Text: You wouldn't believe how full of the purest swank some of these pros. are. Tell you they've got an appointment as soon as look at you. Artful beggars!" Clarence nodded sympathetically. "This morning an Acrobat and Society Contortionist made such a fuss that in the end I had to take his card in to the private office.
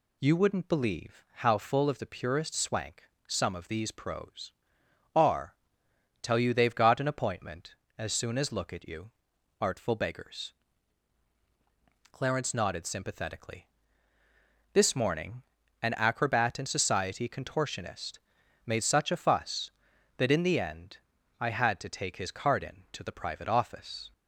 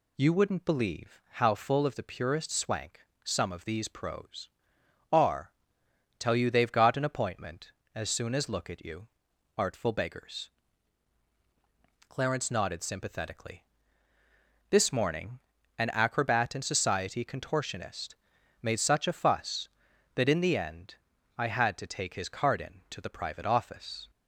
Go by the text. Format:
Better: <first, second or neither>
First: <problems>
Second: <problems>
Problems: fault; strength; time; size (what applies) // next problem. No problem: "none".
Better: neither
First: pauses between "swank" and "some"; slight; at 3.0 s; 0.24 s long // pauses between "morning" and "an"; at 15.4 s; 0.40 s long // pauses between "Contortionist" and "made"; noticeable; at 18.1 s; 0.48 s long // pauses between "end" and "I"; at 20.9 s; 0.42 s long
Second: pauses between "swank" and "some"; slight; at 3.0 s; 0.24 s long // pauses between "morning" and "an"; at 15.3 s; 0.39 s long // pauses between "Contortionist" and "made"; noticeable; at 18.1 s; 0.48 s long // pauses between "end" and "I"; at 20.9 s; 0.42 s long